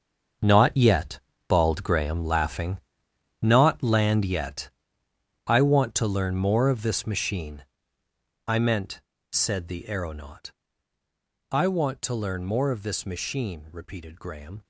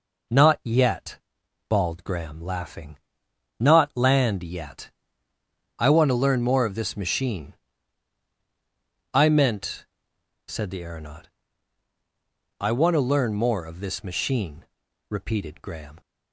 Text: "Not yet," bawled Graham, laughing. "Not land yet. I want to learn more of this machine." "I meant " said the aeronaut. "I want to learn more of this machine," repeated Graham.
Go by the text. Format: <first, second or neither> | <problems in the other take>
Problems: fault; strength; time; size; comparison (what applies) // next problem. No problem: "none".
second | gets quieter; strong; throughout; 13 dB